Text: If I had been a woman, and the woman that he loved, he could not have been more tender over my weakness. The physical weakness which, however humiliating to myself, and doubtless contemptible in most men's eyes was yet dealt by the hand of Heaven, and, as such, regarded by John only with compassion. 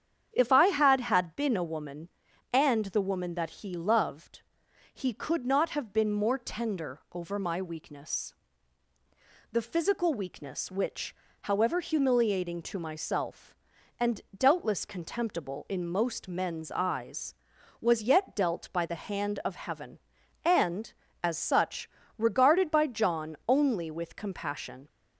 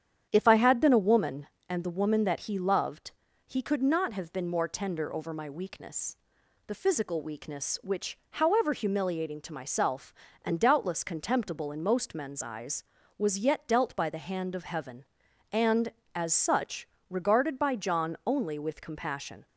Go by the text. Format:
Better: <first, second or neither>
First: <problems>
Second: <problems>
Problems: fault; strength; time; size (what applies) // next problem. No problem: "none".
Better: second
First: starts louder than the rest; strong; until 1.3 s; 8.5 dB // says "had" twice; at 1.0 s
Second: starts louder than the rest; strong; until 1.3 s; 9 dB